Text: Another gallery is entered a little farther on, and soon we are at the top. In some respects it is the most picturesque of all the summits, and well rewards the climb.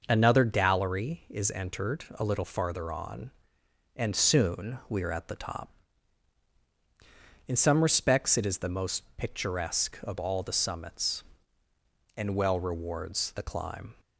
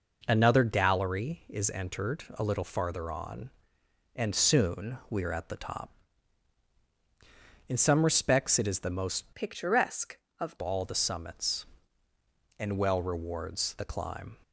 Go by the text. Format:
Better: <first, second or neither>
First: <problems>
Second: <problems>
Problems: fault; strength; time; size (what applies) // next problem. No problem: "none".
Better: first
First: none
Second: changes voice from "picturesque" to "of"; from 9.3 to 10.5 s; 1.2 s long